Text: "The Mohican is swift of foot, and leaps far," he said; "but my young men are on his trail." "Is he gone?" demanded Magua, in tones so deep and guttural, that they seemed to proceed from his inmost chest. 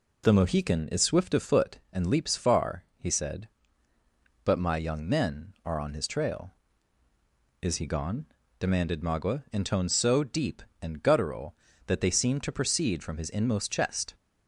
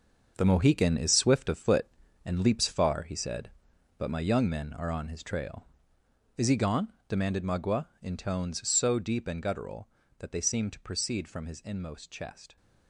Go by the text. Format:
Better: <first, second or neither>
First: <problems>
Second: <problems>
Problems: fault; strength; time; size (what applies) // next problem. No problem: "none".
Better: first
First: none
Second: gets quieter; strong; throughout; 10.5 dB